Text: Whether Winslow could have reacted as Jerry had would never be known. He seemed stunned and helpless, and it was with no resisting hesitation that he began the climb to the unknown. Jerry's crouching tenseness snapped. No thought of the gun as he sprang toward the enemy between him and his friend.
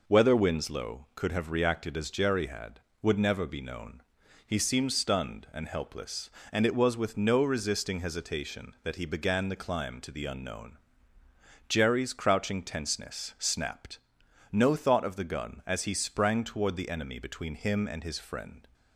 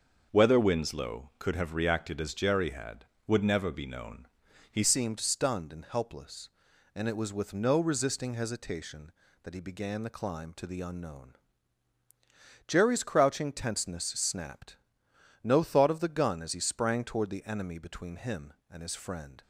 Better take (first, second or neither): first